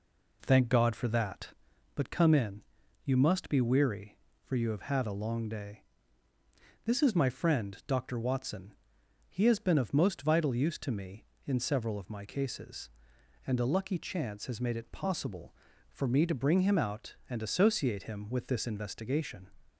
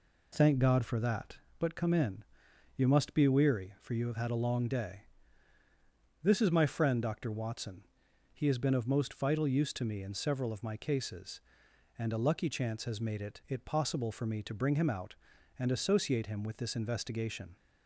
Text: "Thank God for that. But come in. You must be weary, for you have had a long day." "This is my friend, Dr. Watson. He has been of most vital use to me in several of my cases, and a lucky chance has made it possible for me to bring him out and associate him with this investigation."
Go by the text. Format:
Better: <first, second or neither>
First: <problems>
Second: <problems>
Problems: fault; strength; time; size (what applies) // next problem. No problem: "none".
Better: first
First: none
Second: says "it" twice; at 13.4 s